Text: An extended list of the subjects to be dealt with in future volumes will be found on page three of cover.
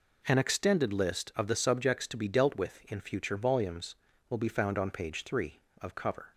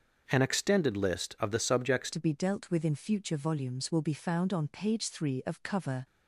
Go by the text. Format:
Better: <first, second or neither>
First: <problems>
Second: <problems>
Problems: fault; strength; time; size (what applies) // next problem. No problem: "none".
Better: first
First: none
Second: starts louder than the rest; until 1.2 s; 6.5 dB // changes voice at "to"; from 2.1 s on; 3.9 s long